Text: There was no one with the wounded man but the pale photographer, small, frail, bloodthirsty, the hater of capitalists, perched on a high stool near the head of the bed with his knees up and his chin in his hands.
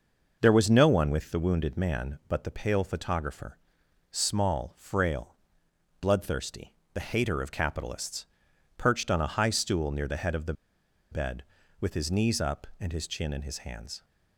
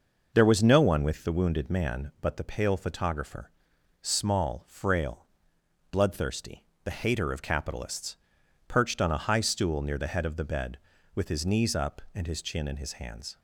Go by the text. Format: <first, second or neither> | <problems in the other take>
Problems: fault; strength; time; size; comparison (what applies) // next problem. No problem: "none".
second | pauses between "the" and "bed"; noticeable; at 10.5 s; 0.58 s long